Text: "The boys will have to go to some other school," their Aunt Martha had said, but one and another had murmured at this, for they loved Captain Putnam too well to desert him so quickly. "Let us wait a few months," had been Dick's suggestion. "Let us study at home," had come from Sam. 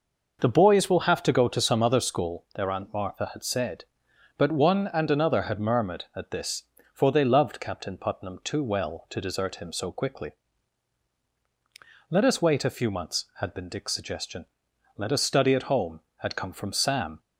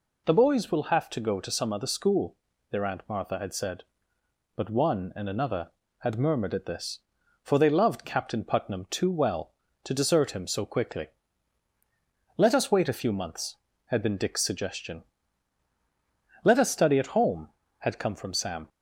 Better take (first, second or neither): neither